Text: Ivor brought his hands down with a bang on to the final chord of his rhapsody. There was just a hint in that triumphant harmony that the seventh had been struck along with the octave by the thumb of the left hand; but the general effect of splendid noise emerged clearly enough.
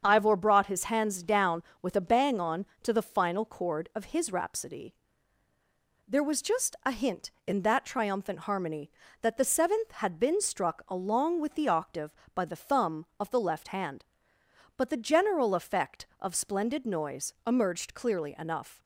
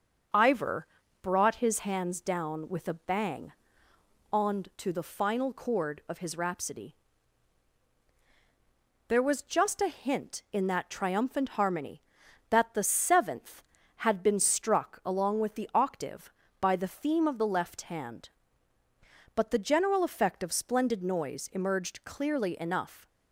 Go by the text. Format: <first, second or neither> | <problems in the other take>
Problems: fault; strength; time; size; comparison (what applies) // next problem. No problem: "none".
first | starts louder than the rest; until 1.7 s; 6.5 dB; strong in the first // pauses between "Ivor" and "brought"; slight; at 0.8 s; 0.36 s long // says "theme" for "thumb"; at 16.8 s